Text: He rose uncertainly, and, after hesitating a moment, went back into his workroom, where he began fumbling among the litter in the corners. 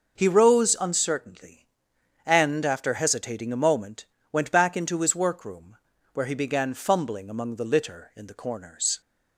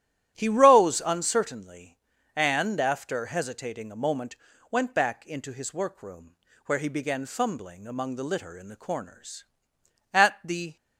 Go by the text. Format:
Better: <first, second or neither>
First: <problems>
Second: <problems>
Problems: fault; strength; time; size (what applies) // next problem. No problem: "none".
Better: first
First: none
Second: starts louder than the rest; strong; until 1.3 s; 12.5 dB // goes on to say "At the"; noticeable; from 10.1 s on; 0.64 s long